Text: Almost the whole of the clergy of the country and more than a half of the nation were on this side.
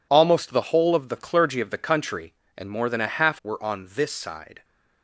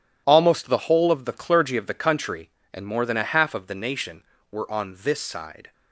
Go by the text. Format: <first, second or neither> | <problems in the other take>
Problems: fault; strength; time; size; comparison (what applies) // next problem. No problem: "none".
second | skips "of the nation"; at 3.4 s